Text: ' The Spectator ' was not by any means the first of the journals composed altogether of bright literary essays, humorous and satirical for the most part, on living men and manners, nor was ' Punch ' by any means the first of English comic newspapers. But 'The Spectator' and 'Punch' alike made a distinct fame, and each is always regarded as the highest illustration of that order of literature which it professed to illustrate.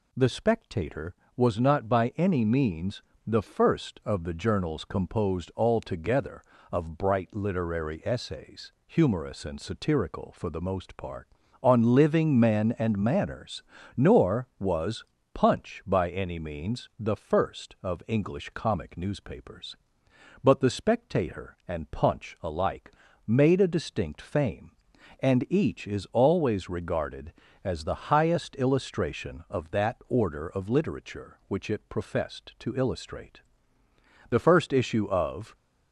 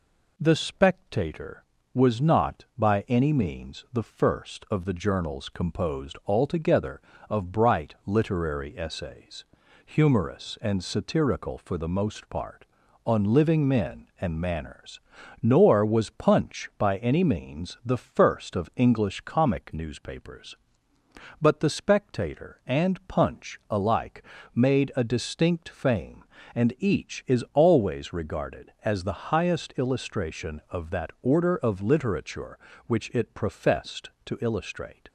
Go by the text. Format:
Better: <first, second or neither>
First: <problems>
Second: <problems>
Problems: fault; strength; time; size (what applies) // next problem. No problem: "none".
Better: second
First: pauses between "means" and "the"; slight; at 3.0 s; 0.26 s long // pauses between "alike" and "made"; slight; at 22.9 s; 0.34 s long // goes on to say "The first issue of"; noticeable; from 34.2 s on; 1.2 s long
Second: pauses between "alike" and "made"; slight; at 24.2 s; 0.30 s long